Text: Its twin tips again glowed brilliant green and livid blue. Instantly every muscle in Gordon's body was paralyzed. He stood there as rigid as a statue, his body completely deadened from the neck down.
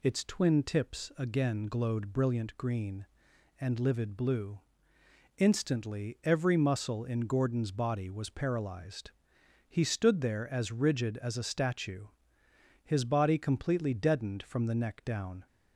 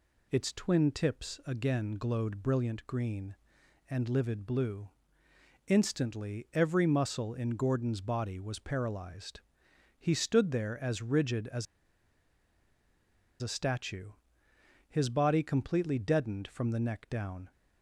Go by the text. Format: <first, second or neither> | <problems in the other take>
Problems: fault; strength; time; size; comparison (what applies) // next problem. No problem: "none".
first | pauses between "as" and "a"; strong; at 11.6 s; 1.7 s long